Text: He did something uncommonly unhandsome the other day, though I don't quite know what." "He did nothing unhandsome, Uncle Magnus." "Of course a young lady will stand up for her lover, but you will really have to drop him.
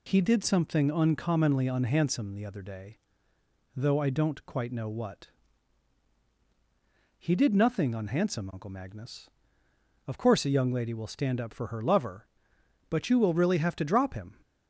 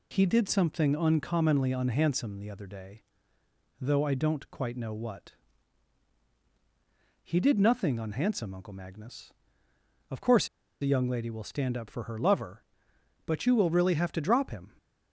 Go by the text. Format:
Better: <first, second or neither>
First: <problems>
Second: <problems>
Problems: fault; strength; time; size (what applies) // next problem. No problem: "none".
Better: first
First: none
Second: pauses between "course" and "a"; slight; at 10.4 s; 0.35 s long